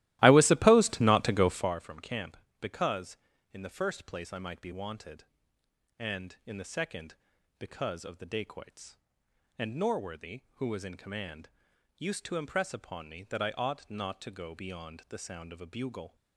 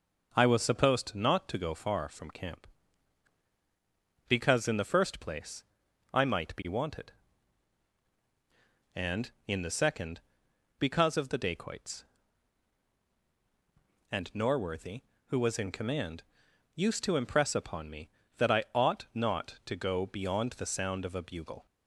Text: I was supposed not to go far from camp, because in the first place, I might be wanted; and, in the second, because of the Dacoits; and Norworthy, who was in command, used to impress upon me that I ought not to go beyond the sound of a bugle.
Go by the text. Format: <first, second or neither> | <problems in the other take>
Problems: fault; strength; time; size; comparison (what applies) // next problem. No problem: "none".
second | starts louder than the rest; strong; until 1.8 s; 16 dB